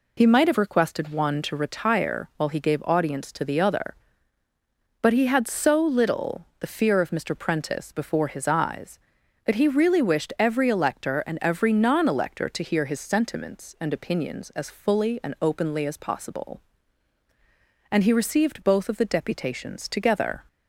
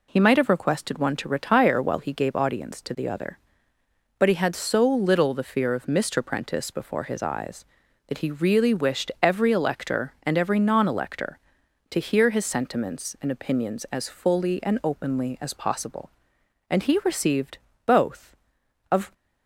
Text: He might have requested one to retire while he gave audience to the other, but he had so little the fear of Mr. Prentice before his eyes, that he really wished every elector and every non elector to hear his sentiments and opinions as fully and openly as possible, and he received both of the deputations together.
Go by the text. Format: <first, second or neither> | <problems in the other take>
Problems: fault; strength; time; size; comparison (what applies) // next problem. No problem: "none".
first | pauses between "received" and "both"; slight; at 17.5 s; 0.28 s long // stops before "the deputations together"; at 19.1 s